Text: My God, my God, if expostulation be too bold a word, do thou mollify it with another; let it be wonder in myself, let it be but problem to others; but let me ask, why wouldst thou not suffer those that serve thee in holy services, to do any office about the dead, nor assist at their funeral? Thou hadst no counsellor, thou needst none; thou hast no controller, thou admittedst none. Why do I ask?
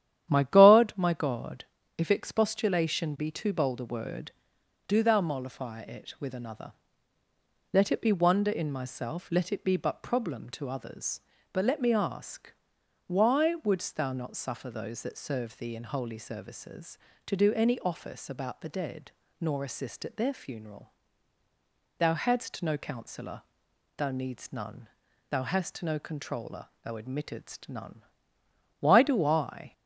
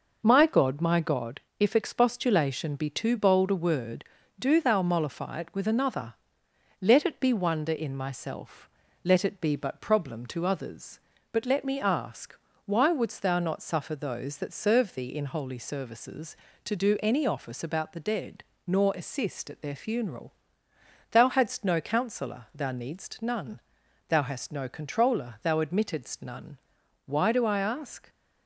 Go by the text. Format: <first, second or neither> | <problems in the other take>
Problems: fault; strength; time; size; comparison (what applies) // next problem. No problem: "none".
second | starts louder than the rest; strong; until 1.3 s; 11 dB // stops before "ask"; at 29.7 s